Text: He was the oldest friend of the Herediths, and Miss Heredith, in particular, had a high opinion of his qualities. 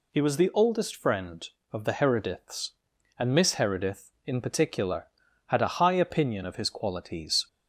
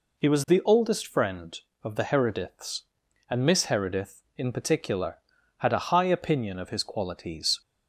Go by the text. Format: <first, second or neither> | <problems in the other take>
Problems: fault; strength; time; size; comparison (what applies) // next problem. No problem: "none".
first | starts louder than the rest; until 1.3 s; 3.5 dB